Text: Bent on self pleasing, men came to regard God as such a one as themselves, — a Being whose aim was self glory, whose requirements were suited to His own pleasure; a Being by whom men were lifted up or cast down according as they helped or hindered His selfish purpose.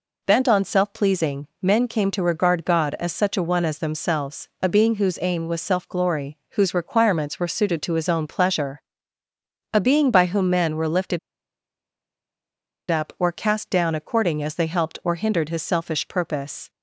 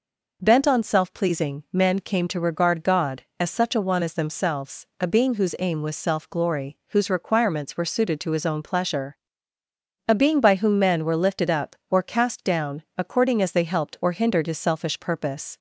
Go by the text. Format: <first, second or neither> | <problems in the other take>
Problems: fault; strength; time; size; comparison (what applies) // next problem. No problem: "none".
second | pauses between "lifted" and "up"; strong; at 11.1 s; 1.7 s long